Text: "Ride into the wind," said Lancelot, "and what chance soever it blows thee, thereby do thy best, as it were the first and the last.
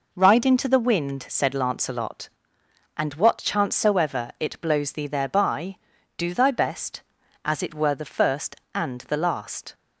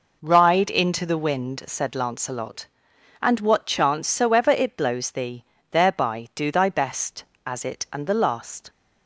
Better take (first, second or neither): first